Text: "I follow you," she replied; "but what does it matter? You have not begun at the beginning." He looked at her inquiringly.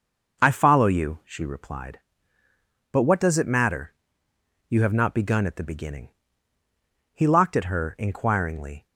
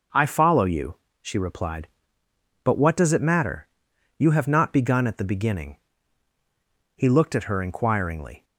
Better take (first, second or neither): second